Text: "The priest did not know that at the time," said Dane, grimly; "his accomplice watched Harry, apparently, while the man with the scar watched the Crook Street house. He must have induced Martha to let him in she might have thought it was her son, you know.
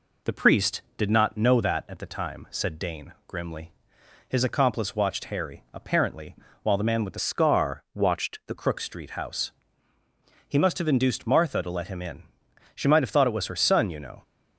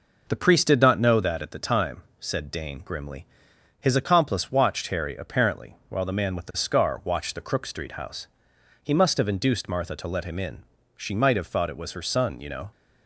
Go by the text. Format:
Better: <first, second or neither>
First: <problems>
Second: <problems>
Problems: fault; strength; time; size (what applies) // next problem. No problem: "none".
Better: second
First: changes voice from "scar" to "the"; from 7.1 to 8.5 s; 1.4 s long // pauses between "in" and "she"; noticeable; at 12.2 s; 0.52 s long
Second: pauses between "in" and "she"; slight; at 10.6 s; 0.32 s long